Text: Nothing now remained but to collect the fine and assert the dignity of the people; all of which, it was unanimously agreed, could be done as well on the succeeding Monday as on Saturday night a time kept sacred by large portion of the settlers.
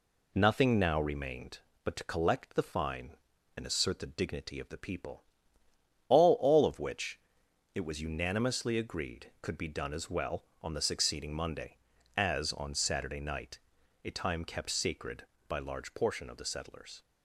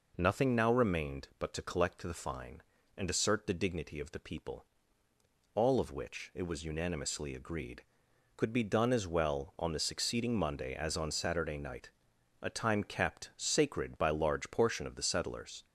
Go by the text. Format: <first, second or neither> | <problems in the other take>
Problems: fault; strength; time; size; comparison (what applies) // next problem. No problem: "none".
second | says "all" twice; at 6.3 s // pauses between "night" and "a"; noticeable; at 13.5 s; 0.48 s long; noticeable in the second